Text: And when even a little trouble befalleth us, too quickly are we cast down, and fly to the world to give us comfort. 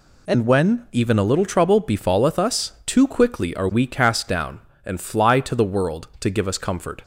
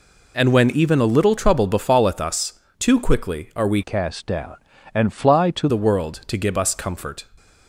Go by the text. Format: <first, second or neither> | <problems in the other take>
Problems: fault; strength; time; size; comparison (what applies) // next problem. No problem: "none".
first | changes voice from "cast" to "to"; from 3.8 to 5.6 s; 1.8 s long